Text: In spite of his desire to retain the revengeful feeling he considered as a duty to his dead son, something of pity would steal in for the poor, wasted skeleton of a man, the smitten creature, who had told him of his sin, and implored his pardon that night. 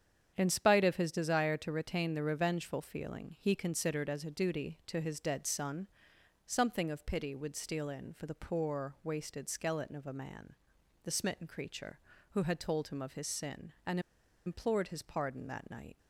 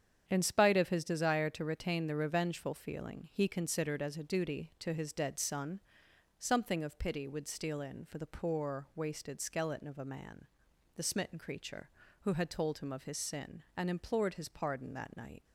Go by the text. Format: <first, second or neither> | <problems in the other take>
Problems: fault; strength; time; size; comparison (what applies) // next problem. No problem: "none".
second | starts louder than the rest; strong; until 1.3 s; 8 dB; strong in the second // pauses between "and" and "implored"; noticeable; at 13.9 s; 0.46 s long